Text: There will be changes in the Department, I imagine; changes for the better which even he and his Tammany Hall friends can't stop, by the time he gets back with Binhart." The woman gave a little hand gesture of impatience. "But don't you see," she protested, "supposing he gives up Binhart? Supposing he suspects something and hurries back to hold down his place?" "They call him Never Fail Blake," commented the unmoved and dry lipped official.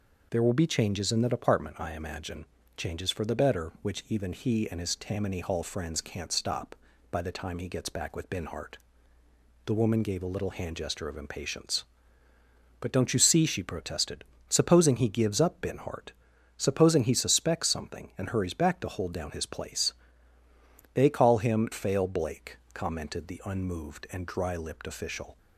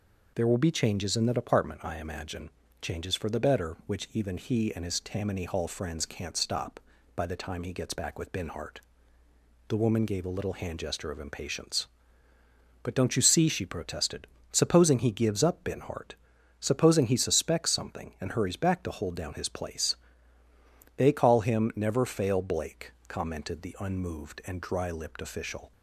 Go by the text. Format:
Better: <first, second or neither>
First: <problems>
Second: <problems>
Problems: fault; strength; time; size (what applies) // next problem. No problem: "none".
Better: second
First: skips "Never"; at 21.7 s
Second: none